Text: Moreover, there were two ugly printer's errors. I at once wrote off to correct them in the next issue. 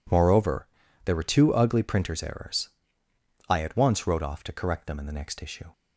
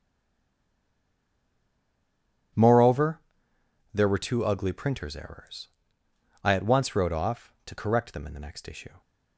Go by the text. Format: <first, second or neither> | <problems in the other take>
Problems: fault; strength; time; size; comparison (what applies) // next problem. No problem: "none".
first | stays silent before the first word; strong; until 2.5 s; 2.5 s long